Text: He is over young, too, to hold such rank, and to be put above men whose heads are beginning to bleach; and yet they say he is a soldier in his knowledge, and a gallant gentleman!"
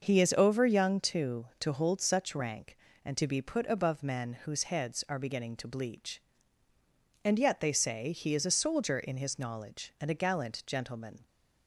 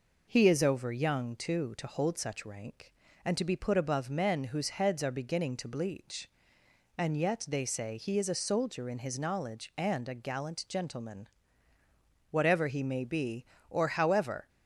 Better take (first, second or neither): first